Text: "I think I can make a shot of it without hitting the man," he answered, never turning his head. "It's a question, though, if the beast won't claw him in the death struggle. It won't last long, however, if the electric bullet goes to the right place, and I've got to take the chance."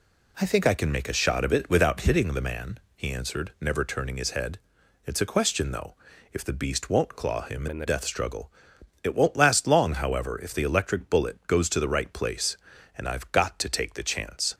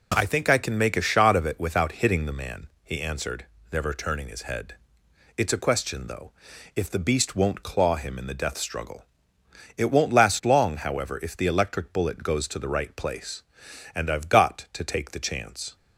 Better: second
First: changes voice from "in" to "the"; from 7.6 to 7.8 s; 0.2 s long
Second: none

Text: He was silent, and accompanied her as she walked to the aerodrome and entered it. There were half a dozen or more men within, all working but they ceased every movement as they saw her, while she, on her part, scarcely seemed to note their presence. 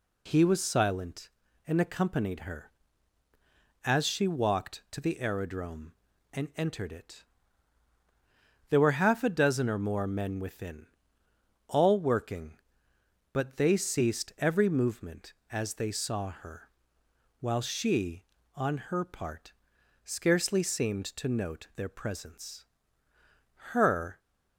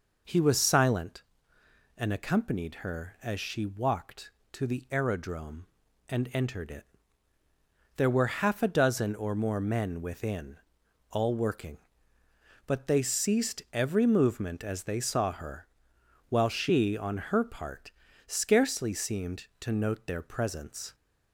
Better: second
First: goes on to say "Her"; slight; from 23.7 s on; 0.48 s long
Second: none

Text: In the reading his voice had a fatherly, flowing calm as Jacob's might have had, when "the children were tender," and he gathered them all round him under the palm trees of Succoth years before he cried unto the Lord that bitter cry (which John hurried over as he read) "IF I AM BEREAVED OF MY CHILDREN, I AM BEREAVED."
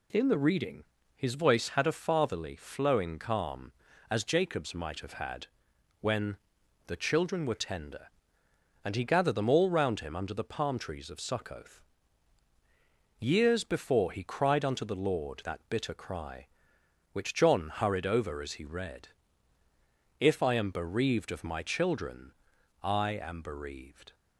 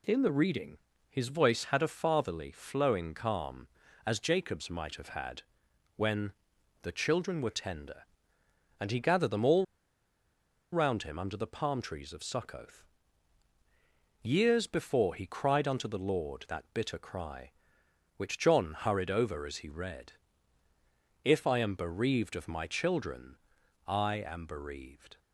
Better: first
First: pauses between "reading" and "his"; slight; at 0.8 s; 0.32 s long // pauses between "when" and "the"; noticeable; at 6.3 s; 0.50 s long // pauses between "Succoth" and "years"; strong; at 11.8 s; 1.3 s long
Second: pauses between "reading" and "his"; slight; at 0.7 s; 0.32 s long // pauses between "when" and "the"; noticeable; at 6.3 s; 0.50 s long // pauses between "all" and "round"; at 9.6 s; 1.0 s long // pauses between "Succoth" and "years"; strong; at 12.8 s; 1.3 s long

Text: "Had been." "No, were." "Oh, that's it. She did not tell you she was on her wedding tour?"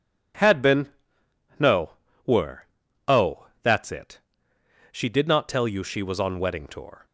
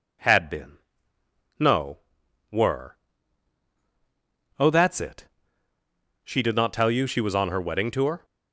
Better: second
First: skips "her"; at 6.3 s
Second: none

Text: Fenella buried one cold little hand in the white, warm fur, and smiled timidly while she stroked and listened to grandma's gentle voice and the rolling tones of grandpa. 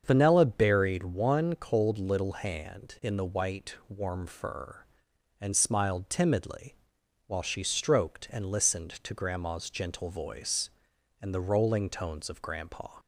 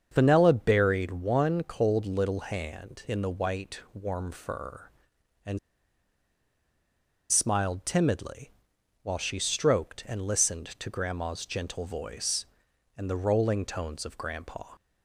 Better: first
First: starts louder than the rest; until 1.0 s; 7 dB // pauses between "timidly" and "while"; noticeable; at 6.7 s; 0.50 s long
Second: starts louder than the rest; until 1.1 s; 7 dB // pauses between "and" and "smiled"; strong; at 5.5 s; 1.7 s long // pauses between "timidly" and "while"; noticeable; at 8.5 s; 0.50 s long

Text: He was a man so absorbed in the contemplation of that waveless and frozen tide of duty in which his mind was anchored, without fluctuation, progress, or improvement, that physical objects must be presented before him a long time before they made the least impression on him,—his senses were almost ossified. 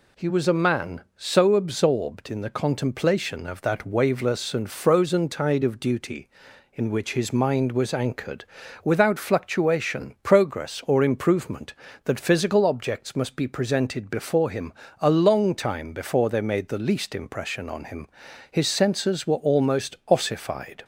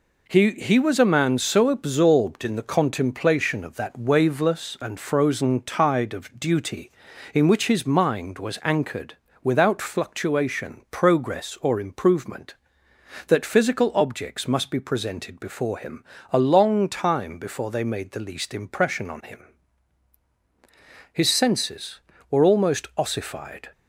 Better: first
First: pauses between "him" and "a"; slight; at 14.7 s; 0.26 s long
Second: says "He" twice; at 0.5 s // pauses between "him" and "a"; slight; at 16.0 s; 0.28 s long

